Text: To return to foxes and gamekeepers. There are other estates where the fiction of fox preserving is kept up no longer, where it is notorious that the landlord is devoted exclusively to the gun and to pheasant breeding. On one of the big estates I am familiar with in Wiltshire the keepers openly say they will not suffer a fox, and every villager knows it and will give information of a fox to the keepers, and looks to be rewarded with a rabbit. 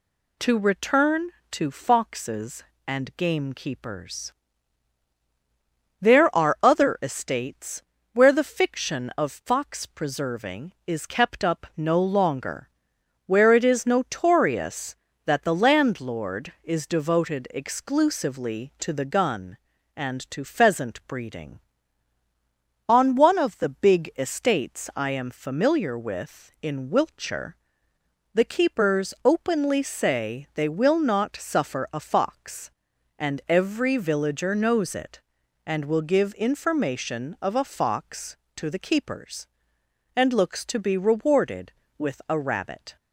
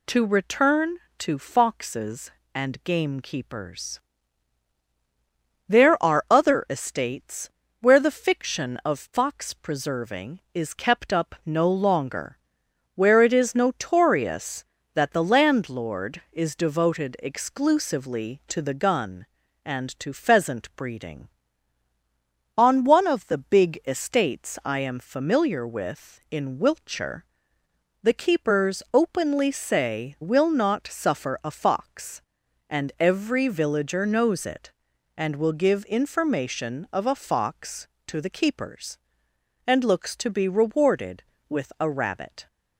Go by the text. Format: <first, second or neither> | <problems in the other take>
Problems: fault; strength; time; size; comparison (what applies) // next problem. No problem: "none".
first | pauses between "estates" and "where"; slight; at 7.4 s; 0.32 s long; slight in the first // pauses between "Wiltshire" and "the"; noticeable; at 27.2 s; 0.80 s long; noticeable in the first // skips "they"; at 30.1 s